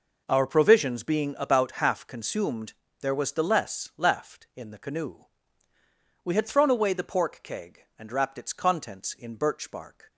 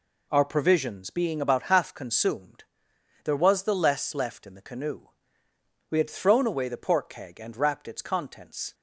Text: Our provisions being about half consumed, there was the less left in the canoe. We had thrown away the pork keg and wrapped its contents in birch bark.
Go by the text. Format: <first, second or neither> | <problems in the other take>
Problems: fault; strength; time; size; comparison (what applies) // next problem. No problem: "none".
first | stops before "in birch bark"; at 8.7 s